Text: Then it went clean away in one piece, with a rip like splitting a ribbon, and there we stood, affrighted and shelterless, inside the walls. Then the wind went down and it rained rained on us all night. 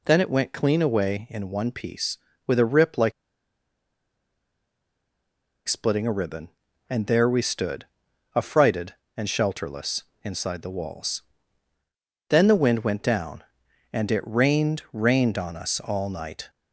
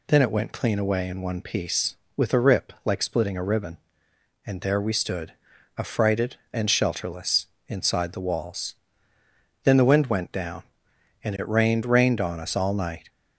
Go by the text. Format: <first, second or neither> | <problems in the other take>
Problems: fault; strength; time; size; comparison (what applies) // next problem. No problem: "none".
second | pauses between "like" and "splitting"; strong; at 3.1 s; 2.5 s long